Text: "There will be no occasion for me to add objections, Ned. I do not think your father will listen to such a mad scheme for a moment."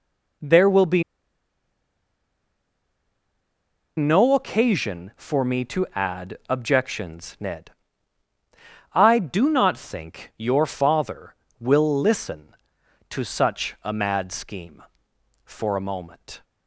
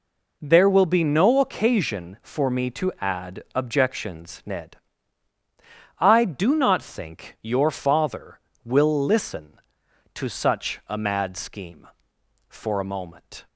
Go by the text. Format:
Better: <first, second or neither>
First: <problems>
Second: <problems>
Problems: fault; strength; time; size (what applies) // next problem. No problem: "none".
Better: second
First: pauses between "be" and "no"; strong; at 1.0 s; 2.9 s long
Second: none